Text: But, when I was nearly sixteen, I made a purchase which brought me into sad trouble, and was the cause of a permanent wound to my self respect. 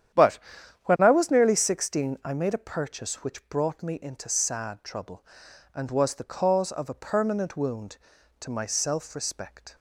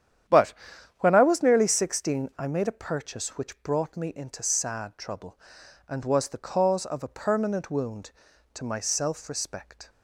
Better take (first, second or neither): neither